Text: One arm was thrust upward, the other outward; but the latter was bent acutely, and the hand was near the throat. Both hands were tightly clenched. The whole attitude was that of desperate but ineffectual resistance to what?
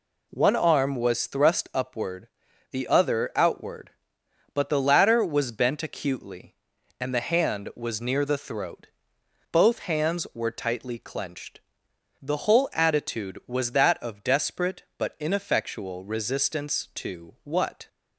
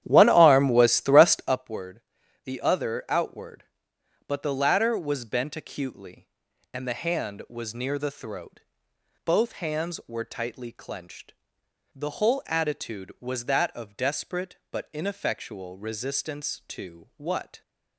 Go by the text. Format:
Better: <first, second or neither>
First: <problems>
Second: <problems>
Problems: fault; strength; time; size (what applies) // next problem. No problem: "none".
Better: first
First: none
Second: starts louder than the rest; strong; until 1.7 s; 11 dB